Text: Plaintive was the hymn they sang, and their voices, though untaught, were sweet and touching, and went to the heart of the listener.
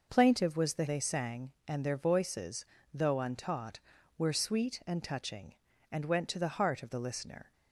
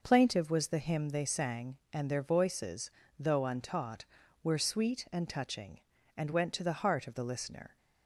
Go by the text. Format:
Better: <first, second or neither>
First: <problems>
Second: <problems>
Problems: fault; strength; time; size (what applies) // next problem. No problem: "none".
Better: second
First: skips "hymn"; at 0.8 s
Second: none